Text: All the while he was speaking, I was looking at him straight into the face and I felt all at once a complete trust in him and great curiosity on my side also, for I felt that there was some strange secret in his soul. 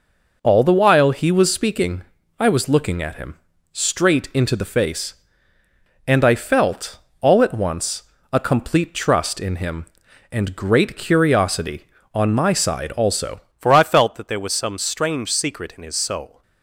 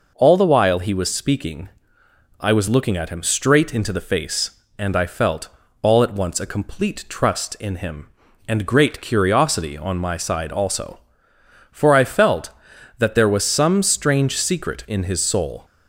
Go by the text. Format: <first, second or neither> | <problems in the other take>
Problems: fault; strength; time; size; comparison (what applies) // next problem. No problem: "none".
second | pauses between "him" and "straight"; at 3.3 s; 0.38 s long // pauses between "felt" and "all"; slight; at 6.9 s; 0.22 s long; slight in the second // pauses between "once" and "a"; slight; at 8.0 s; 0.28 s long // changes voice at "for"; from 13.5 s on; 2.9 s long